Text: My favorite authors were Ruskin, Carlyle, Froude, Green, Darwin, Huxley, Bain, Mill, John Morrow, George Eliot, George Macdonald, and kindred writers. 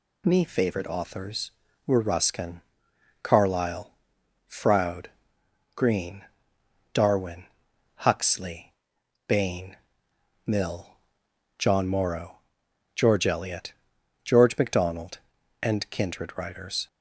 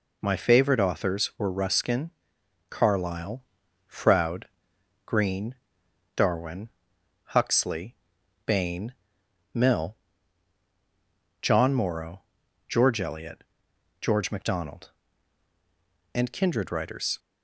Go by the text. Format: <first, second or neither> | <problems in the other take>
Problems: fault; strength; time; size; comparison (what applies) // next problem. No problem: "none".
second | says "Me" for "My"; at 0.2 s